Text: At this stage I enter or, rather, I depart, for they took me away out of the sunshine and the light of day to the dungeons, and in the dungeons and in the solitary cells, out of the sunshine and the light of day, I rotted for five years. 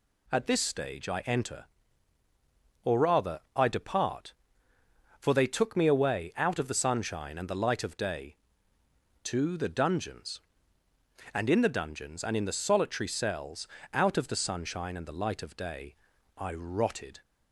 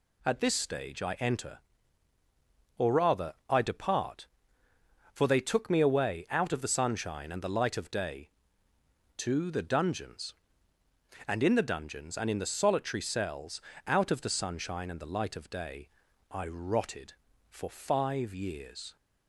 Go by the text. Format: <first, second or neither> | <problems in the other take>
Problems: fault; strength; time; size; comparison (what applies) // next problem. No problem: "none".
second | stops before "for five years"; at 17.2 s